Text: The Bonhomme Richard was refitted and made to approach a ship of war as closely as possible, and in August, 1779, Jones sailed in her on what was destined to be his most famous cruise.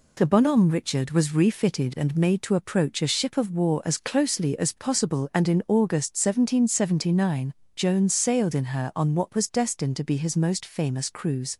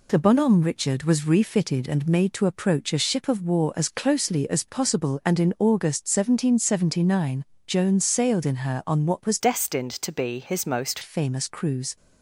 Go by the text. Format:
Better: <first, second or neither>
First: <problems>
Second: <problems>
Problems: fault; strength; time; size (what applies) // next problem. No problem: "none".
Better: first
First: none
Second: changes voice from "destined" to "most"; from 9.3 to 10.9 s; 1.6 s long